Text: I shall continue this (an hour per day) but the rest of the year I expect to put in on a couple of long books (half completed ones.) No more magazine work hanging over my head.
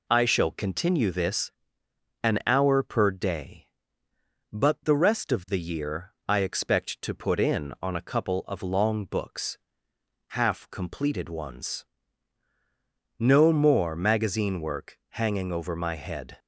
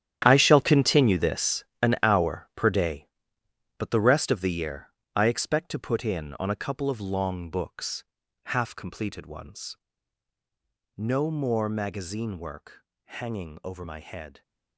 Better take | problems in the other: first | gets quieter; strong; throughout; 13 dB // pauses between "year" and "I"; slight; at 4.8 s; 0.28 s long // pauses between "work" and "hanging"; slight; at 12.8 s; 0.24 s long

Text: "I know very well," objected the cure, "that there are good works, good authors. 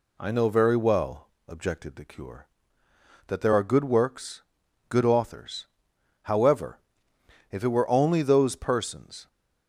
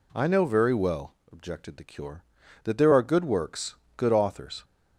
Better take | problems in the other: second | goes on to say "However if it were only those persons"; strong; from 6.2 s on; 3.0 s long

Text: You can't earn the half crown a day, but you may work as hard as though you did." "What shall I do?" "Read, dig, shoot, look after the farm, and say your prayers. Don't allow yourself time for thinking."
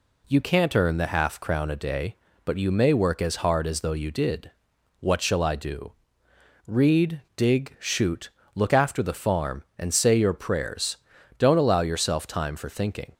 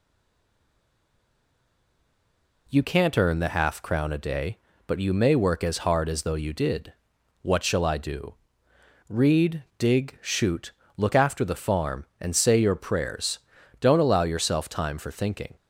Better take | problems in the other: first | stays silent before the first word; strong; until 2.6 s; 2.6 s long

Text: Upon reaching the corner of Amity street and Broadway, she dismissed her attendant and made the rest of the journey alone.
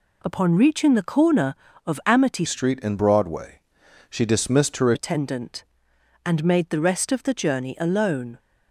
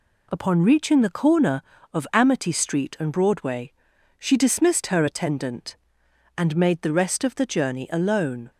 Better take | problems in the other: second | changes voice from "street" to "her"; from 2.4 to 4.9 s; 2.5 s long

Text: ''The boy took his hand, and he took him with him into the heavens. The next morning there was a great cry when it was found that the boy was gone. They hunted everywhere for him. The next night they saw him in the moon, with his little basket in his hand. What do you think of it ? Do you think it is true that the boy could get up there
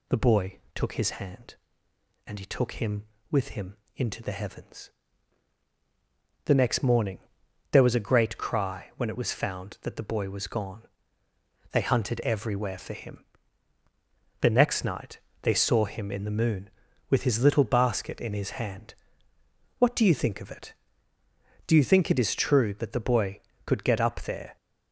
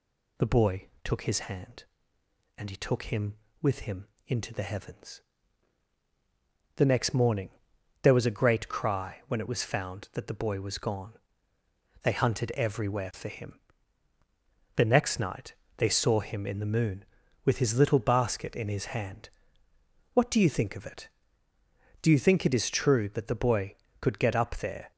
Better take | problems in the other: neither | pauses between "boy" and "took"; slight; the same in both // pauses between "him" and "into"; slight; the same in both // pauses between "morning" and "there"; noticeable; the same in both // pauses between "night" and "they"; slight; the same in both

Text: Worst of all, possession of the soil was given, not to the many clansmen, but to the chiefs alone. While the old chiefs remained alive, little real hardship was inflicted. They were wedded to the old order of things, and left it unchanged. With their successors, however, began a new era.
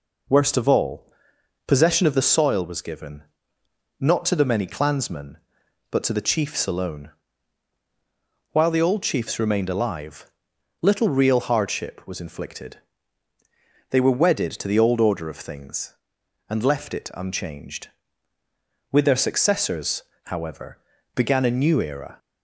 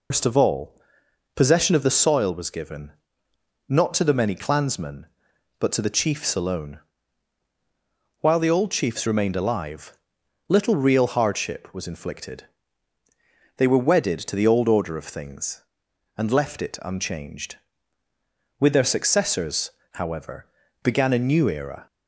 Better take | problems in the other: first | loses the start of "Worst"; at 0.1 s; 125 ms

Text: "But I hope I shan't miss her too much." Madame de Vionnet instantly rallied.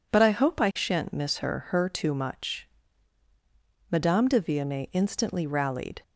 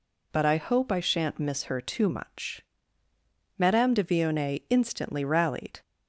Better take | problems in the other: second | says "her" twice; at 1.6 s

